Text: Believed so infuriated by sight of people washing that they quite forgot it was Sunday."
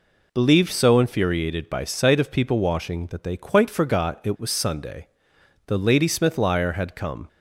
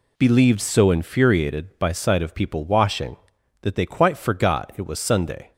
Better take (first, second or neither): second